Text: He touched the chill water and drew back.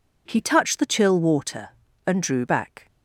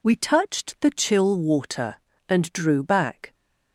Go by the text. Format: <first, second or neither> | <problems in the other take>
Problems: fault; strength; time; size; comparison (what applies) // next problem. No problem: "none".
first | says "We" for "He"; at 0.0 s